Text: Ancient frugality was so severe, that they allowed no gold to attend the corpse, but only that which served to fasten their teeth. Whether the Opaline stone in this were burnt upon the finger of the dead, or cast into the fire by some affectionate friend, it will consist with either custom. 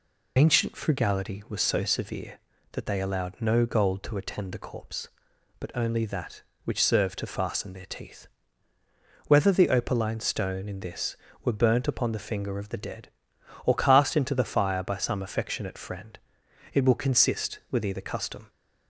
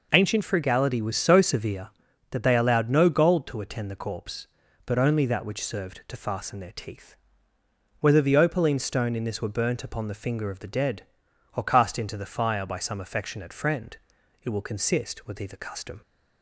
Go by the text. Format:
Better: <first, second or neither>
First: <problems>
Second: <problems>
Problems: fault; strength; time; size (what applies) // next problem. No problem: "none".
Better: second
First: loses the start of "Ancient"; at 0.3 s; 70 ms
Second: none